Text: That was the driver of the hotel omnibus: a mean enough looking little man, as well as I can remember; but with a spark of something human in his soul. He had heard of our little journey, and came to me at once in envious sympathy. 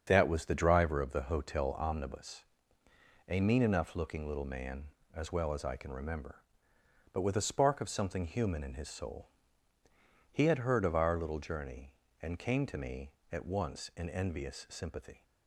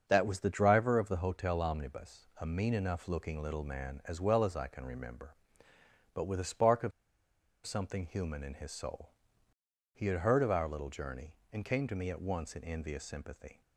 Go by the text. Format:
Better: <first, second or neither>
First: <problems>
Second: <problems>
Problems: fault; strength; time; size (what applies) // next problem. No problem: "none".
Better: first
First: starts louder than the rest; strong; until 1.0 s; 7 dB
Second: starts louder than the rest; until 1.0 s; 6.5 dB // pauses between "of" and "something"; noticeable; at 6.9 s; 0.73 s long